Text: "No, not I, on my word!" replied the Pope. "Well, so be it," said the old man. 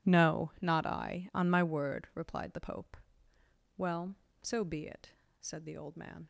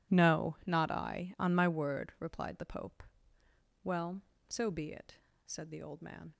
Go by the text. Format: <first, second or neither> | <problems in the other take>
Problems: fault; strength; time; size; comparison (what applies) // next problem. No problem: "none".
neither | none